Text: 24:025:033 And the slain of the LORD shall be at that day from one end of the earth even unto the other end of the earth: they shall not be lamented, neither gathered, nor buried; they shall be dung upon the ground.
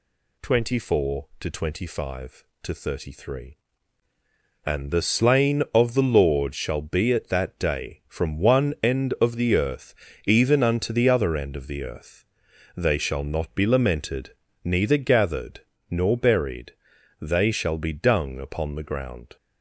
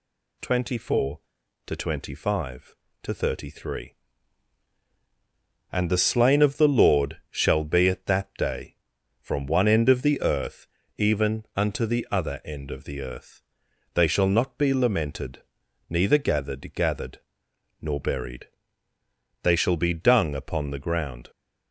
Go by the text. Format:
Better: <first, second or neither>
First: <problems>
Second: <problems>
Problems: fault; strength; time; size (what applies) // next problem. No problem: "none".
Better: first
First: pauses between "earth" and "even"; slight; at 9.9 s; 0.28 s long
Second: pauses between "earth" and "even"; slight; at 10.6 s; 0.30 s long // says "gathered" twice; at 16.7 s